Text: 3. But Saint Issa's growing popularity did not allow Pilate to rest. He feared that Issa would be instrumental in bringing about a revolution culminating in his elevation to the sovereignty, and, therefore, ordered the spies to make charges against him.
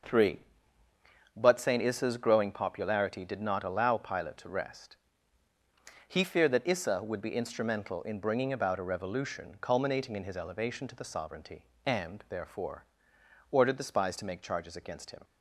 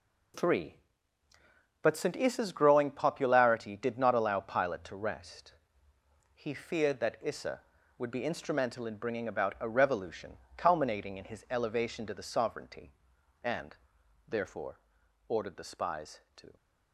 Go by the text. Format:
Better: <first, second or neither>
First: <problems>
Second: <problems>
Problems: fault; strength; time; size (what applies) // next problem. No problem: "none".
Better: first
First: none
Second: pauses between "revolution" and "culminating"; slight; at 10.3 s; 0.20 s long // stops before "make charges against him"; at 16.5 s